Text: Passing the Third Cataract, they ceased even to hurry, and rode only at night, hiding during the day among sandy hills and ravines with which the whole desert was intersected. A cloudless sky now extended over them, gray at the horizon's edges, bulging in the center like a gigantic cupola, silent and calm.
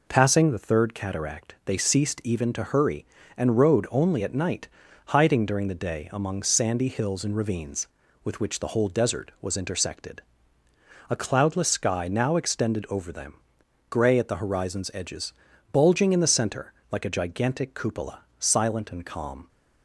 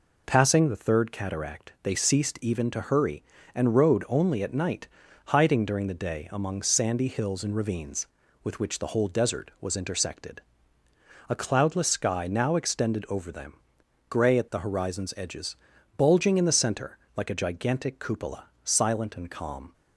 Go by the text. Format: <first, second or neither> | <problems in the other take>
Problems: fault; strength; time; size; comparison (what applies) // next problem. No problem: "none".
neither | pauses between "center" and "like"; slight; the same in both